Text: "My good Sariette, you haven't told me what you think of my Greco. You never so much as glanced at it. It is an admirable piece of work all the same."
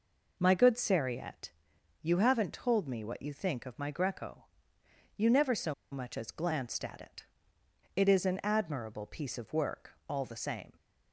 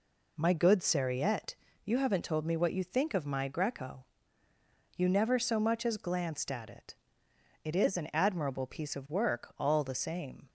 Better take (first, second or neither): second